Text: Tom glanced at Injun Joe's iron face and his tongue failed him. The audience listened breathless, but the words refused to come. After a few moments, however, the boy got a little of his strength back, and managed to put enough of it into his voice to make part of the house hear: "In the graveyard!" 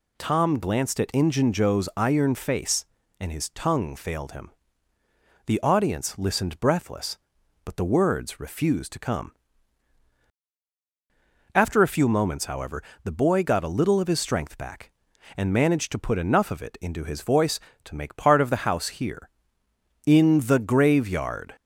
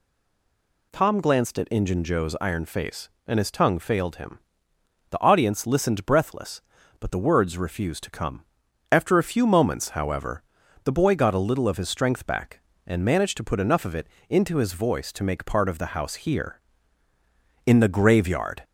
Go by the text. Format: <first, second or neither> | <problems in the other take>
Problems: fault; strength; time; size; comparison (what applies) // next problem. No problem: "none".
first | stays silent before the first word; slight; until 0.9 s; 0.9 s long // pauses between "it" and "into"; slight; at 14.0 s; 0.22 s long